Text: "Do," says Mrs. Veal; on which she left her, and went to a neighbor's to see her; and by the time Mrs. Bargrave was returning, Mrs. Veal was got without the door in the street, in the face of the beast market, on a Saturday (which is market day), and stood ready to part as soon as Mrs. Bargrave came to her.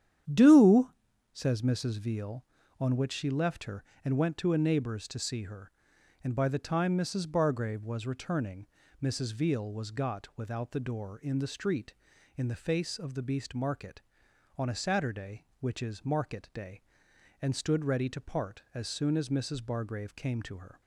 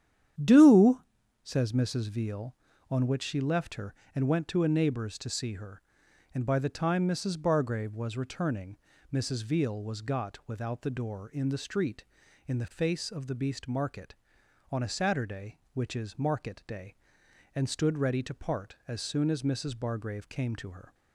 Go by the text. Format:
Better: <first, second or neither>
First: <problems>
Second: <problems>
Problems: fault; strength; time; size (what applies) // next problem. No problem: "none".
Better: neither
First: starts louder than the rest; strong; until 1.7 s; 9.5 dB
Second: starts louder than the rest; strong; until 1.8 s; 9.5 dB